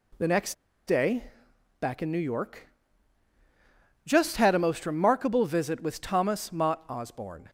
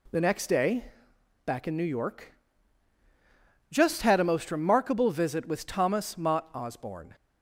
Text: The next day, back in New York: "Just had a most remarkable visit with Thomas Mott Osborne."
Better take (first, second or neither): second